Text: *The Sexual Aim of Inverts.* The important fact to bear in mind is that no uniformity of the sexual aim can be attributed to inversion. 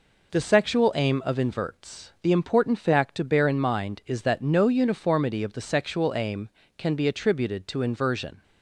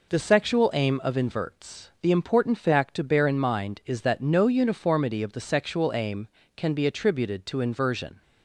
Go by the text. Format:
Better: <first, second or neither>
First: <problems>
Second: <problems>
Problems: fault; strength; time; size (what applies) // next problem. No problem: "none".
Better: neither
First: none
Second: none